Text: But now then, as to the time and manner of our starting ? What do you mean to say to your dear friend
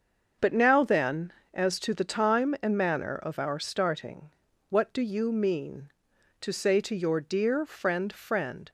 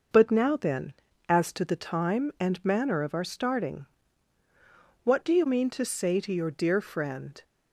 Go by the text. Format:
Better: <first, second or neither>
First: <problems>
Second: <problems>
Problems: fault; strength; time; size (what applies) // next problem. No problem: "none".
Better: second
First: starts louder than the rest; until 1.6 s; 6.5 dB // says "friend" twice; at 8.1 s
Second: none